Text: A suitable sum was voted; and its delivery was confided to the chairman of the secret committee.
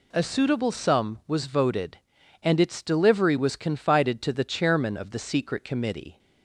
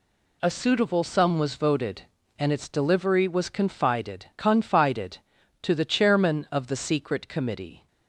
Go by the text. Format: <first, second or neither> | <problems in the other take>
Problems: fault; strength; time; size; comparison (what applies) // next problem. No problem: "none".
first | says "confided" twice; at 4.3 s